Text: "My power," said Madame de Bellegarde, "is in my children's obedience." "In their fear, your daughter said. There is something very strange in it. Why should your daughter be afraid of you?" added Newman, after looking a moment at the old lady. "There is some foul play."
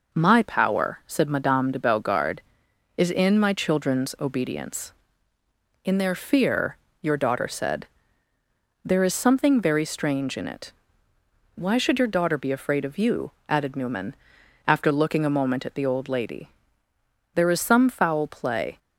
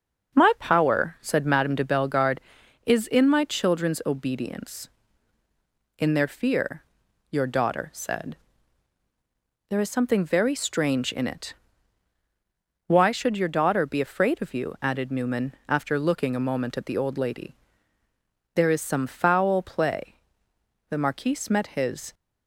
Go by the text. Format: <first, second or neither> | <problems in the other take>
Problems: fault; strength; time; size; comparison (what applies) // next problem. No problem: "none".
first | starts louder than the rest; until 1.4 s; 6 dB // goes on to say "The marquise met his"; noticeable; from 20.8 s on; 1.2 s long